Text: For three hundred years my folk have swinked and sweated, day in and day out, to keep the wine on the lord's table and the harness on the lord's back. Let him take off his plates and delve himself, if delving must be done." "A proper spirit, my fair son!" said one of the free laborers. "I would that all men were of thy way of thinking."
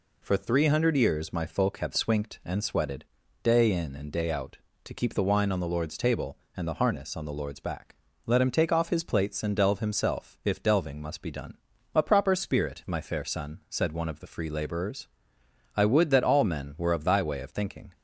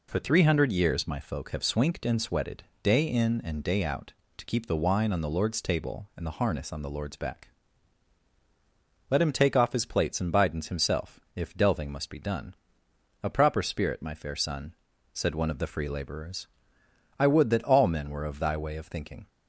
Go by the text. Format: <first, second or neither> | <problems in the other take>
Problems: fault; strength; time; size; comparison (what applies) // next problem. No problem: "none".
first | says "bidens" for "delve"; at 10.3 s